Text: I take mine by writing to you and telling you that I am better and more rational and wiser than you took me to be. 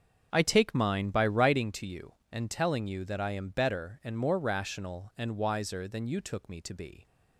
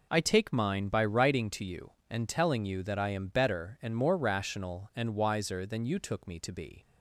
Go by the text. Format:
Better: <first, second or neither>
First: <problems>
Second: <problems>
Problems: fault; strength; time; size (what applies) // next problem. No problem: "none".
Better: second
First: starts louder than the rest; strong; until 1.7 s; 7 dB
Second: none